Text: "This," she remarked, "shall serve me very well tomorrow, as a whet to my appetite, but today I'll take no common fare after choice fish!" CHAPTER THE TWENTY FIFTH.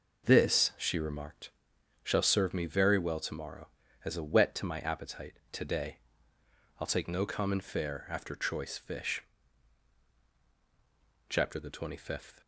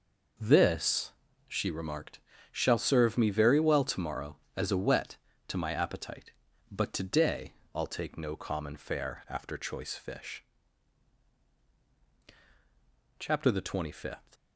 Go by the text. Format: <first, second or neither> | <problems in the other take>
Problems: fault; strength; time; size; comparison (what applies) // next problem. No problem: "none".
second | skips "but"; at 5.4 s // pauses between "today" and "I'll"; noticeable; at 5.9 s; 0.80 s long; slight in the second